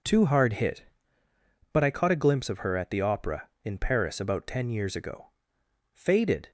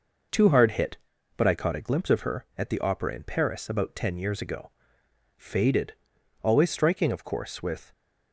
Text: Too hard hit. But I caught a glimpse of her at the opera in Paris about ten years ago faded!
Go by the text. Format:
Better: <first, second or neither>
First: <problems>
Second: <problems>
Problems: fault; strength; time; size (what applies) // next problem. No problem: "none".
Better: first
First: pauses between "ago" and "faded"; noticeable; at 5.2 s; 0.66 s long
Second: pauses between "ago" and "faded"; noticeable; at 4.6 s; 0.68 s long // goes on to say "Always striking of course with"; from 6.4 s on; 1.4 s long